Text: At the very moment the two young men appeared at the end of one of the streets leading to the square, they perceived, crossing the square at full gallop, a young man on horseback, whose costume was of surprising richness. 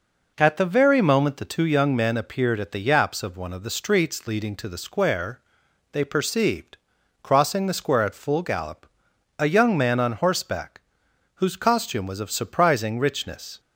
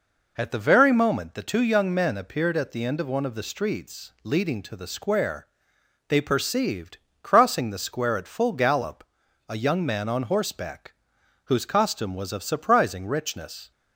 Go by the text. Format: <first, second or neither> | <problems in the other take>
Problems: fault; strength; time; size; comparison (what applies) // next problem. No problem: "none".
second | says "yaps" for "end"; at 2.7 s